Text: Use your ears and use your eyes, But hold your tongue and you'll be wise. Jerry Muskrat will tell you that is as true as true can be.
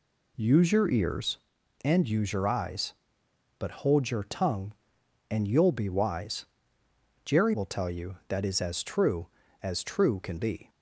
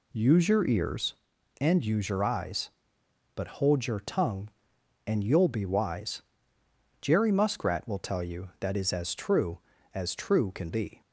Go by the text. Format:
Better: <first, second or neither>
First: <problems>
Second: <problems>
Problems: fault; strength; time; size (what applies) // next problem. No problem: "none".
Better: second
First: skips "Muskrat"; at 7.5 s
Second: none